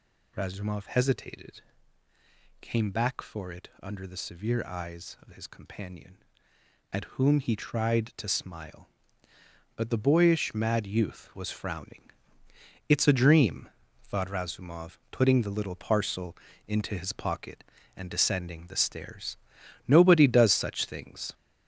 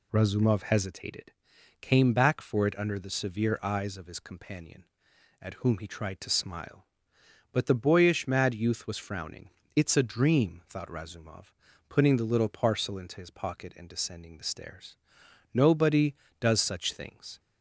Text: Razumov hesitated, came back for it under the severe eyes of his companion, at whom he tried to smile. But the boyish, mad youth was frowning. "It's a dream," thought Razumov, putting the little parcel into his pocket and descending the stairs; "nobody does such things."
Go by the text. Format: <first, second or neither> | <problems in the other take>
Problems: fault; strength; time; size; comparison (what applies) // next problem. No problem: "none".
second | gets louder; noticeable; throughout; 5 dB // pauses between "parcel" and "into"; slight; at 16.3 s; 0.30 s long